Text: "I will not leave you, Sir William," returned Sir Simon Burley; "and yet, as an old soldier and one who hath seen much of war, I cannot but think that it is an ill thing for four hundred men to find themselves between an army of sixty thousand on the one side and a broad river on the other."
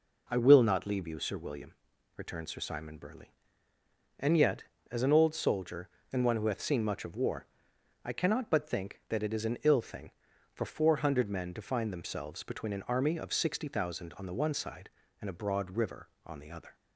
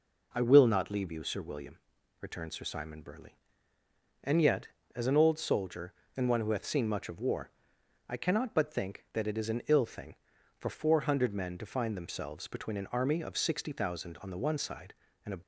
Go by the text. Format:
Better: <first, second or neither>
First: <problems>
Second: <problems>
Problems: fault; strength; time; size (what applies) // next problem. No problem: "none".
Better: first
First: none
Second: stops before "broad river on the other"; at 15.4 s